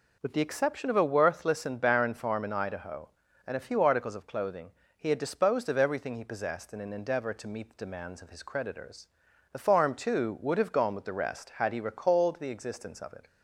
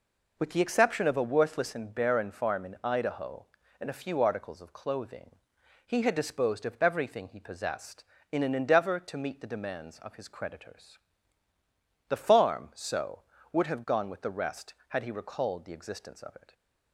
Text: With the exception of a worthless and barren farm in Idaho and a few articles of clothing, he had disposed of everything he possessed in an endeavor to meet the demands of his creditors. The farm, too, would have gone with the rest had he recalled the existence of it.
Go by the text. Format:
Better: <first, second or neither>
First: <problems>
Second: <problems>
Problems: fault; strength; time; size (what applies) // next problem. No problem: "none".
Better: first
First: none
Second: says "so" for "too"; at 12.7 s